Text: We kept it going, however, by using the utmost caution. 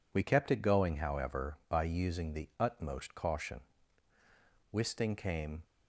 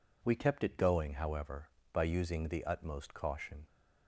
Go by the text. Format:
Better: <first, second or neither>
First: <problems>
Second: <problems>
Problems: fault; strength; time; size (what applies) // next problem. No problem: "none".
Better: second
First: goes on to say "Wisting came"; noticeable; from 4.7 s on; 0.90 s long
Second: none